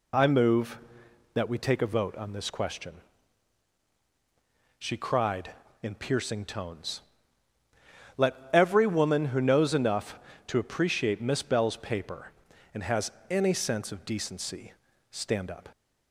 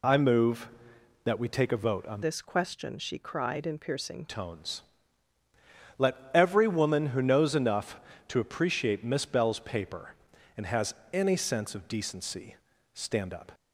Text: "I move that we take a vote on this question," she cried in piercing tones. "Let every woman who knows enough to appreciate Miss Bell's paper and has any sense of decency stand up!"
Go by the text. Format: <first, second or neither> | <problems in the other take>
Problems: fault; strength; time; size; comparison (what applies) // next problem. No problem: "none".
first | changes voice from "this" to "piercing"; from 2.2 to 4.2 s; 2.0 s long // pauses between "Let" and "every"; slight; at 6.1 s; 0.18 s long; slight in the first // pauses between "has" and "any"; slight; at 10.9 s; 0.16 s long; slight in the first // pauses between "decency" and "stand"; at 12.5 s; 0.38 s long; also in the first